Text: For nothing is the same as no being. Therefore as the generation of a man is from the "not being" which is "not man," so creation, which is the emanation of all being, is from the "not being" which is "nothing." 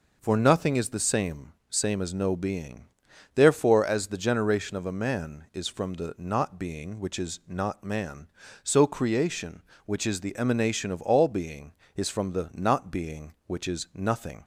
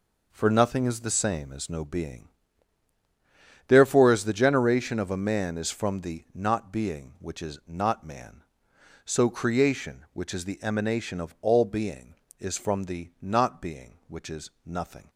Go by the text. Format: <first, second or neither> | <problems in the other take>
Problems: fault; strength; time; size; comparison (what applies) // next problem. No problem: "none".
second | says "same" twice; at 1.7 s